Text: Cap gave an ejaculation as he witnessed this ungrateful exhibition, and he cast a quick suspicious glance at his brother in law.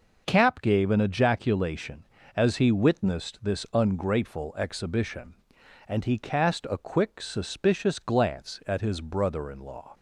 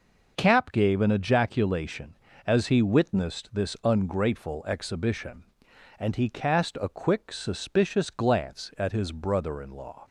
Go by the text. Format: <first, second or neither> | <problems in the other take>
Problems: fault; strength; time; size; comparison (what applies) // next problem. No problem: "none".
neither | none